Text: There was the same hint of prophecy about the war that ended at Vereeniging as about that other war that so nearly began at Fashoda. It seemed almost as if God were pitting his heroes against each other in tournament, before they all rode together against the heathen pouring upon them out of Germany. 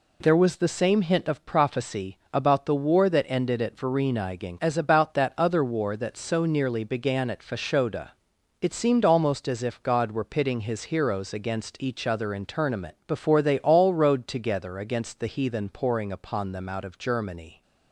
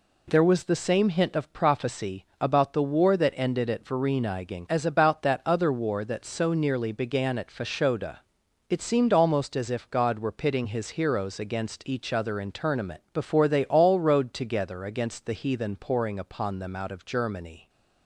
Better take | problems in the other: neither | none

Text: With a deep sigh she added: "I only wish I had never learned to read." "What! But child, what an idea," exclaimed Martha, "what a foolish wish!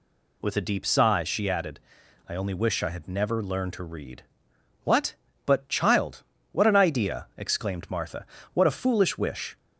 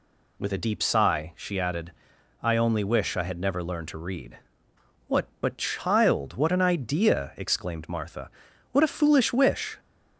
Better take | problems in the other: neither | none

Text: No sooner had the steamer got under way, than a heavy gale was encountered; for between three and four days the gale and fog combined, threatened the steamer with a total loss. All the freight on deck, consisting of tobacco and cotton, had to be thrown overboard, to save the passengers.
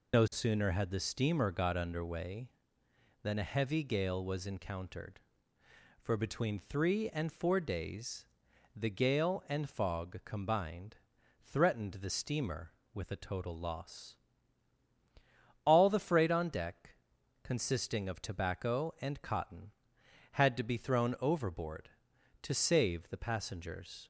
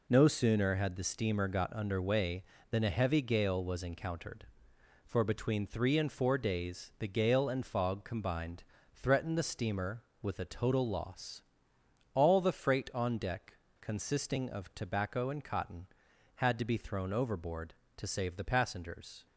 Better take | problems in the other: second | loses the start of "No"; at 0.1 s; 65 ms // pauses between "days" and "the"; noticeable; at 8.2 s; 0.48 s long

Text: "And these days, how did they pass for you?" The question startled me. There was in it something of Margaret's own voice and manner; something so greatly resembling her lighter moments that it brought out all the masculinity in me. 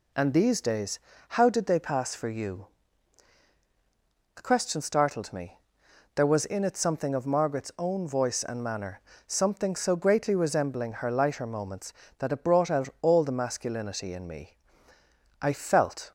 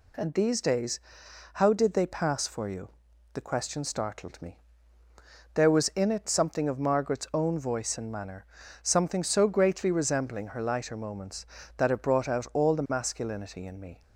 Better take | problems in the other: second | goes on to say "I felt"; noticeable; from 15.4 s on; 0.70 s long

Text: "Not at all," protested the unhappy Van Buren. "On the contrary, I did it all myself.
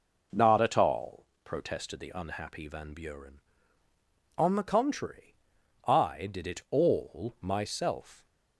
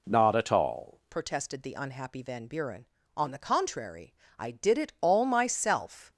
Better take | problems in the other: first | changes voice at "protested"; from 1.1 s on; 5.0 s long

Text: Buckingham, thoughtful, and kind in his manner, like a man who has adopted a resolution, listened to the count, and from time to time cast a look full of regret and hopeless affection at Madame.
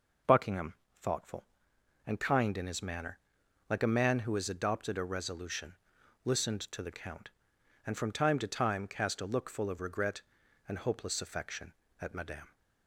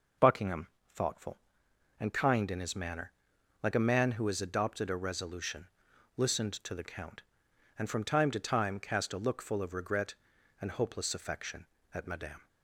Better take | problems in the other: neither | none

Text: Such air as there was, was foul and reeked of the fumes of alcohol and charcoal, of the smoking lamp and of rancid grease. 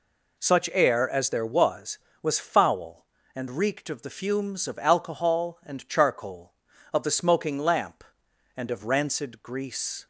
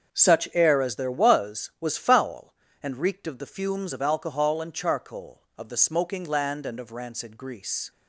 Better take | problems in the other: first | starts louder than the rest; until 1.1 s; 7 dB // says "land" for "lamp"; at 6.2 s

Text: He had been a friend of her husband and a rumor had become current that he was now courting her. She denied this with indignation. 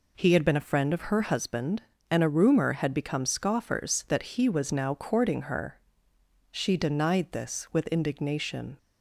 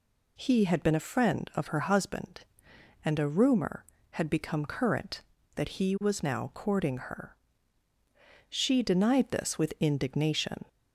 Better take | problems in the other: second | says "scoffers" for "current"; at 3.2 s

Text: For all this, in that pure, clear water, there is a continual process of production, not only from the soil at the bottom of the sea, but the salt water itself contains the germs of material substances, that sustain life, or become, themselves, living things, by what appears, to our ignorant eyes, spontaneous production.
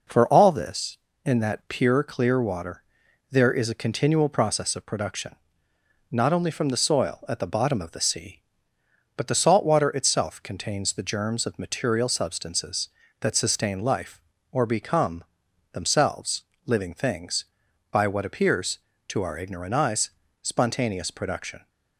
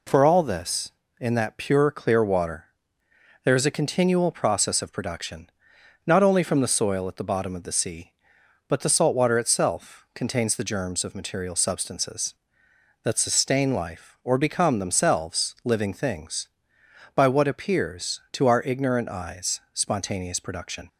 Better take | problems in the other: neither | none

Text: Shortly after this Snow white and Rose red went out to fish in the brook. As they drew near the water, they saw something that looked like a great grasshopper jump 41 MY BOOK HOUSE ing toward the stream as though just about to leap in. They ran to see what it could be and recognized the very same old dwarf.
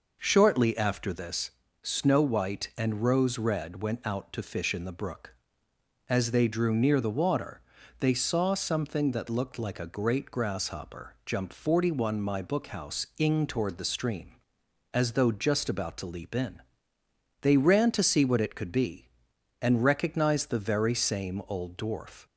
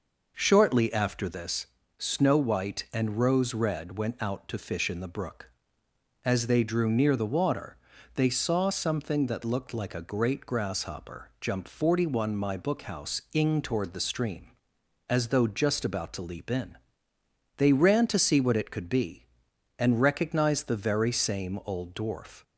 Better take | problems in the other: neither | pauses between "this" and "Snow"; slight; the same in both

